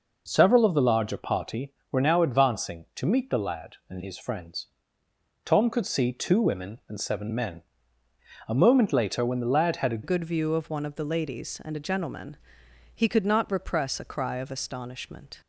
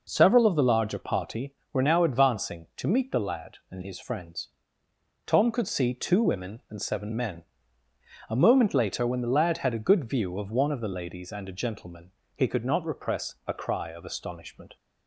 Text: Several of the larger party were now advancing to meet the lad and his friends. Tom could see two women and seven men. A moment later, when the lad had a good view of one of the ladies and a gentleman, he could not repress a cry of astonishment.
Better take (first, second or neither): second